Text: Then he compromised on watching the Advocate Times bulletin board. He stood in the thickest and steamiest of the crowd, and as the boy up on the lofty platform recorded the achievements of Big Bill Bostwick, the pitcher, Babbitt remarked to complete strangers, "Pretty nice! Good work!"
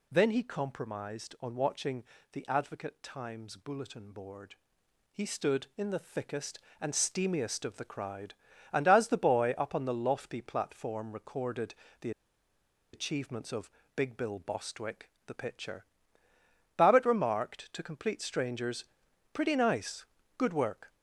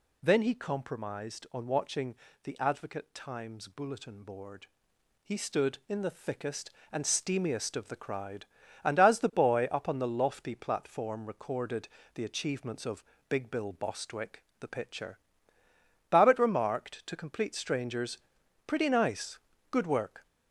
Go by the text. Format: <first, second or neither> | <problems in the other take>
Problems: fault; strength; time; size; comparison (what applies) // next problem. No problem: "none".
second | pauses between "watching" and "the"; slight; at 2.0 s; 0.28 s long; slight in the second // pauses between "recorded" and "the"; slight; at 11.7 s; 0.26 s long; slight in the second // pauses between "the" and "achievements"; noticeable; at 12.1 s; 0.82 s long // pauses between "of" and "Big"; slight; at 13.7 s; 0.24 s long; slight in the second